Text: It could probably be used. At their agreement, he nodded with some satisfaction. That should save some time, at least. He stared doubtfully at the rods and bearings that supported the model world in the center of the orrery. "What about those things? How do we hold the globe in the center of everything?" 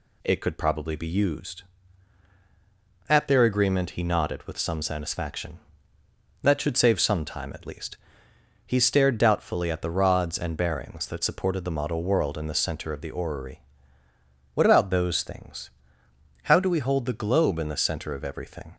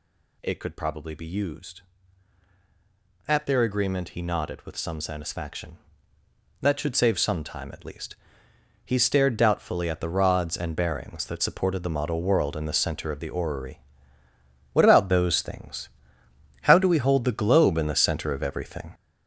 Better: first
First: none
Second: gets louder; strong; throughout; 7.5 dB

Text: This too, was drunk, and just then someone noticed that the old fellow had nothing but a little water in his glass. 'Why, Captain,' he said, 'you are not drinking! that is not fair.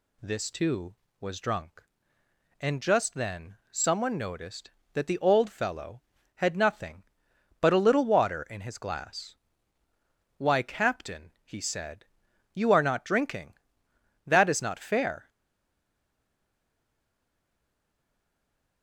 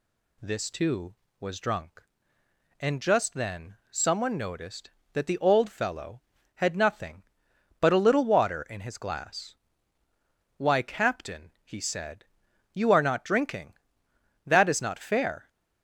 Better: second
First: pauses between "then" and "someone"; slight; at 3.5 s; 0.16 s long // stays silent after the last word; strong; from 15.2 s on; 3.6 s long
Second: pauses between "then" and "someone"; slight; at 3.7 s; 0.16 s long

